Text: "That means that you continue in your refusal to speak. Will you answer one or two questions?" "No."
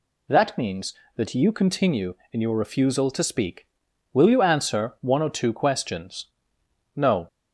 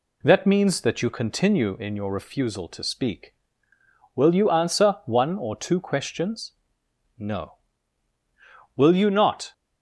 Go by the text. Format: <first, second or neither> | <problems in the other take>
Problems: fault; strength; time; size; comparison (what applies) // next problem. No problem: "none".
first | goes on to say "Will you not"; noticeable; from 8.7 s on; 0.78 s long